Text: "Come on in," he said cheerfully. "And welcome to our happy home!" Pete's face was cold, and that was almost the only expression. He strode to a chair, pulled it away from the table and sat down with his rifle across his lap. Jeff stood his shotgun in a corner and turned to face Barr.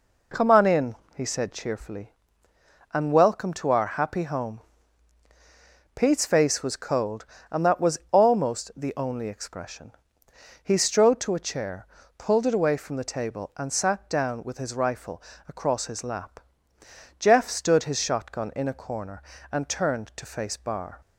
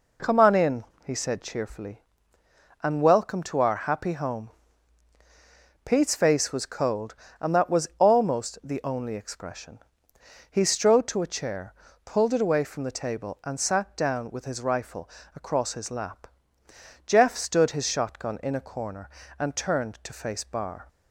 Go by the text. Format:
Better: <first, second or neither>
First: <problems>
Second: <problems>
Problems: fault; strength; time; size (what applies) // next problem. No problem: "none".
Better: neither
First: pauses between "rifle" and "across"; slight; at 15.2 s; 0.24 s long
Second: pauses between "rifle" and "across"; slight; at 15.0 s; 0.24 s long